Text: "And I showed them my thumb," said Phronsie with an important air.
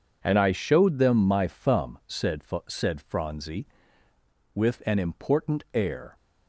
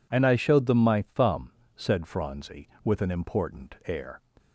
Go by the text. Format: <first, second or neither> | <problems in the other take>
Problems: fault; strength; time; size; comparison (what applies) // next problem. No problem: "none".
second | says "said" twice; at 2.6 s